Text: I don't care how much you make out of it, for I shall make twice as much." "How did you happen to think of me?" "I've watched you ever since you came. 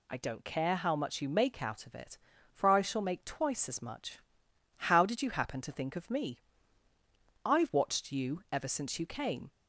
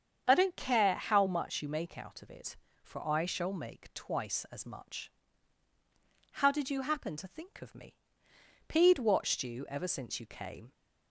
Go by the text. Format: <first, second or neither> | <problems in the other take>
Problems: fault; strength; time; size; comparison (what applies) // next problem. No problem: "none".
first | starts louder than the rest; strong; until 1.2 s; 7.5 dB // says "Pede" for "I've"; at 8.6 s